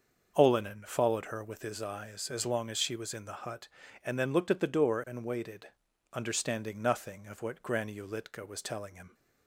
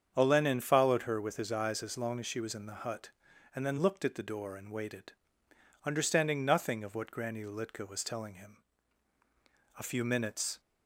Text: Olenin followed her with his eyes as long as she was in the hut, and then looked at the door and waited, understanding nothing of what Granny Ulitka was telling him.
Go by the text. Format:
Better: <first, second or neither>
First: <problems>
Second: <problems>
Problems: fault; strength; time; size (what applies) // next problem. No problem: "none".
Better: first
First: starts louder than the rest; until 1.3 s; 6.5 dB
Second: starts louder than the rest; strong; until 1.1 s; 7.5 dB // goes on to say "A few minutes"; noticeable; from 9.7 s on; 0.82 s long